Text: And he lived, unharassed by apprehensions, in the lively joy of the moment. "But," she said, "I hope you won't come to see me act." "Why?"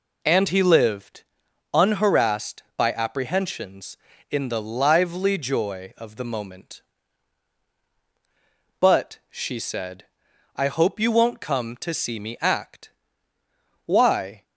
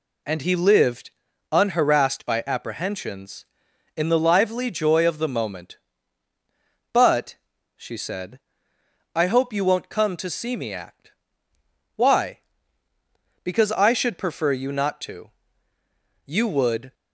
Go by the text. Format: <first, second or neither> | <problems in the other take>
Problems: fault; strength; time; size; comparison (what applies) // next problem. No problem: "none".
first | goes on to say "Because I should prefer you not to You would"; strong; from 13.4 s on; 3.5 s long